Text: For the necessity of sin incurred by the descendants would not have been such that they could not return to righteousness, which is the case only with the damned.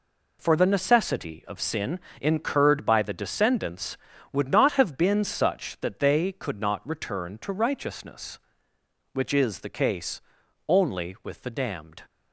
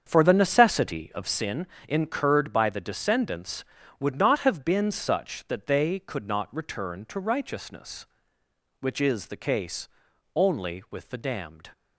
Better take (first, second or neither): first